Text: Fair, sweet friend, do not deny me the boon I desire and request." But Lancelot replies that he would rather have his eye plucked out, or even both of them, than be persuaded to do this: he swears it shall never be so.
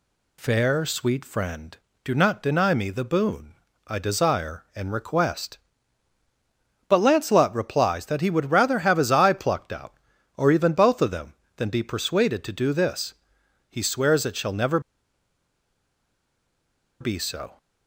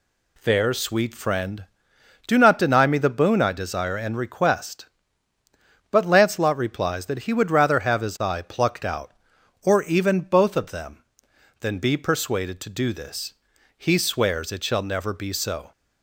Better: second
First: pauses between "boon" and "I"; slight; at 3.5 s; 0.32 s long // pauses between "never" and "be"; strong; at 14.7 s; 2.2 s long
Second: none

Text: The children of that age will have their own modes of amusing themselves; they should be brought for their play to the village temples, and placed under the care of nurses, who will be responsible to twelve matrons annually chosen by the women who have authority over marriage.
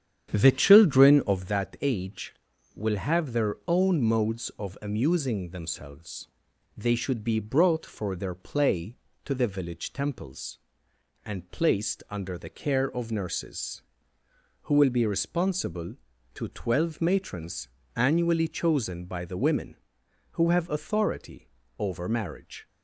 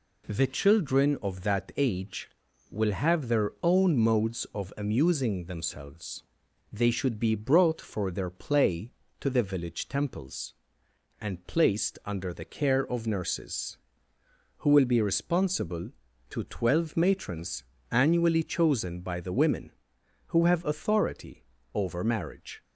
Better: second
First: starts louder than the rest; strong; until 1.5 s; 9 dB // pauses between "matrons" and "annually"; slight; at 17.6 s; 0.28 s long // pauses between "authority" and "over"; slight; at 21.4 s; 0.32 s long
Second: pauses between "matrons" and "annually"; slight; at 17.6 s; 0.28 s long // pauses between "authority" and "over"; slight; at 21.4 s; 0.32 s long

